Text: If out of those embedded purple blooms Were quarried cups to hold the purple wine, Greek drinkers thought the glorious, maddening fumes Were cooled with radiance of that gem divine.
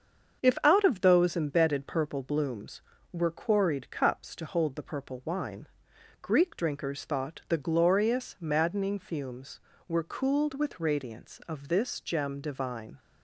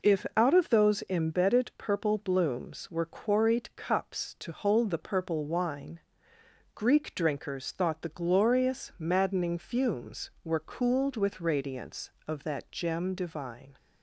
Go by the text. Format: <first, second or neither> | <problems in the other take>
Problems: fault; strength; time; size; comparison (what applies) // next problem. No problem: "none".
second | starts louder than the rest; until 1.4 s; 7 dB // says "this" for "that"; at 11.6 s